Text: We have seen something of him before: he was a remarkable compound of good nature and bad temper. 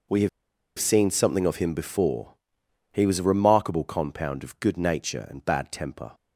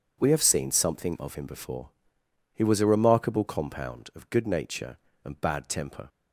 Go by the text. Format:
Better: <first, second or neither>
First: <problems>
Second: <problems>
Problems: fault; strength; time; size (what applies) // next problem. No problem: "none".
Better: second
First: pauses between "have" and "seen"; noticeable; at 0.2 s; 0.49 s long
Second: none